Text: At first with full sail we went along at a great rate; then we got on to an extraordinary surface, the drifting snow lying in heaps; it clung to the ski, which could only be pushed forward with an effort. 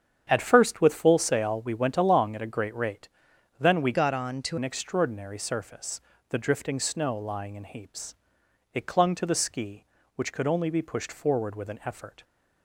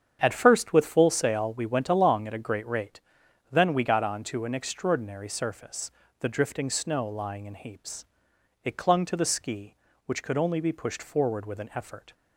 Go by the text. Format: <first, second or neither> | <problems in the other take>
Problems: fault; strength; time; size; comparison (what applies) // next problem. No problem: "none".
second | starts louder than the rest; strong; until 1.3 s; 8 dB; strong in the second // changes voice from "got" to "to"; from 3.9 to 4.5 s; 0.6 s long